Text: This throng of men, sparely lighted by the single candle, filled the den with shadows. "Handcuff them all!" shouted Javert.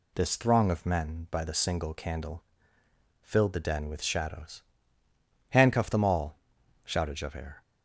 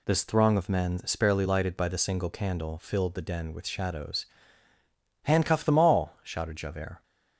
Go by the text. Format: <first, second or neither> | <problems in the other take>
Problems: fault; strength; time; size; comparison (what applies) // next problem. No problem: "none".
second | skips "sparely lighted"; at 1.2 s